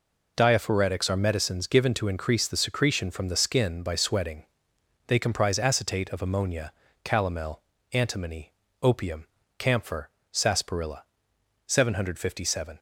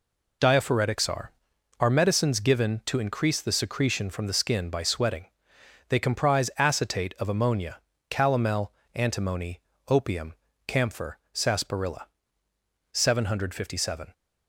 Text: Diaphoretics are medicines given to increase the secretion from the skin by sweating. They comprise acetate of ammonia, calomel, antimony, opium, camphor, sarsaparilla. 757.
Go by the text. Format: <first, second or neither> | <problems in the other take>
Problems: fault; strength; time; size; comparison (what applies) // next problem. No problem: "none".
first | says "are" twice; at 1.7 s